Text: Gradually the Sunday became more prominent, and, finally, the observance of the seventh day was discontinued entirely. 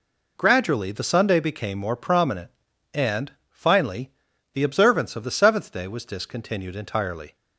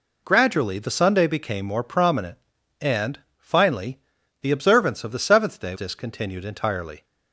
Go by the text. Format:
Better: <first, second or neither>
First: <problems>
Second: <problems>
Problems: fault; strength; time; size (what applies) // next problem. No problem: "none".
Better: first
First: none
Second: skips "was"; at 5.7 s